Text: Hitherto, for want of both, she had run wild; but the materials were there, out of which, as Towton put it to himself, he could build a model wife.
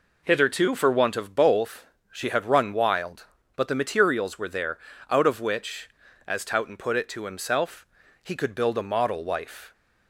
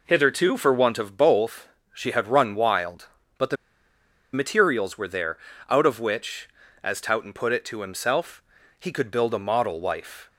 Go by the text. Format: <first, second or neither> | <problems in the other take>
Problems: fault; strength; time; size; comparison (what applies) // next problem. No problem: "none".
first | pauses between "the" and "materials"; noticeable; at 3.5 s; 0.78 s long